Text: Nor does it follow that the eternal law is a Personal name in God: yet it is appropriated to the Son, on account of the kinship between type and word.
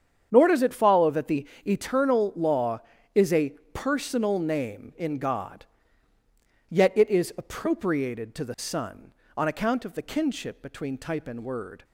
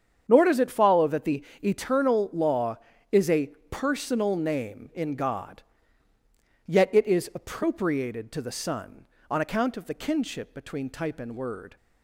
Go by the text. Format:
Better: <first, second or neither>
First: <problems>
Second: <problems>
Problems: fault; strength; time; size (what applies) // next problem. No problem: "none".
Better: neither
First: starts louder than the rest; strong; until 1.3 s; 8 dB // pauses between "the" and "eternal"; slight; at 1.4 s; 0.20 s long // pauses between "a" and "Personal"; slight; at 3.5 s; 0.22 s long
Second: starts louder than the rest; strong; until 1.2 s; 8 dB // pauses between "the" and "eternal"; slight; at 1.4 s; 0.20 s long // pauses between "a" and "Personal"; slight; at 3.4 s; 0.22 s long